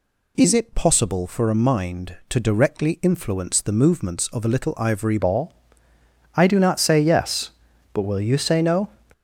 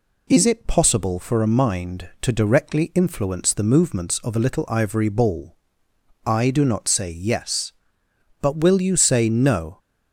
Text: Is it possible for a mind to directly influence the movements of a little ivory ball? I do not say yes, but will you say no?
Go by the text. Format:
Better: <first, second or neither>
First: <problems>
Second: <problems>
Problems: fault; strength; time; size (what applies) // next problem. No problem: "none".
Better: second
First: changes voice at "ball"; from 5.1 s on; 3.7 s long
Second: none